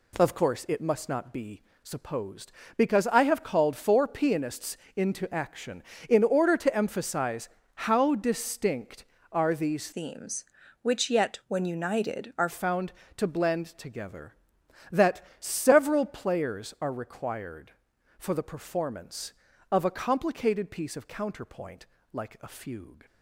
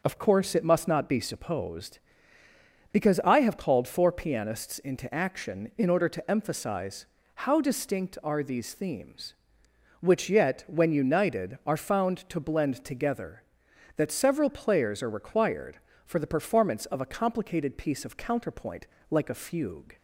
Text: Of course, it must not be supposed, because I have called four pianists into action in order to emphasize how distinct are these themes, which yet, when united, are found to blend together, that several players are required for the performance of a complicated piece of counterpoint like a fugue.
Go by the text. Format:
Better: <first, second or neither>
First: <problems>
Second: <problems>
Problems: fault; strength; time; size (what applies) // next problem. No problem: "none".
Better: second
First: pauses between "be" and "supposed"; slight; at 1.6 s; 0.20 s long // pauses between "pianists" and "into"; slight; at 4.7 s; 0.20 s long // pauses between "emphasize" and "how"; slight; at 7.4 s; 0.26 s long // changes voice from "themes" to "are"; from 9.9 to 12.4 s; 2.5 s long // pauses between "counterpoint" and "like"; slight; at 21.8 s; 0.26 s long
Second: pauses between "emphasize" and "how"; slight; at 7.0 s; 0.30 s long // pauses between "counterpoint" and "like"; slight; at 18.8 s; 0.24 s long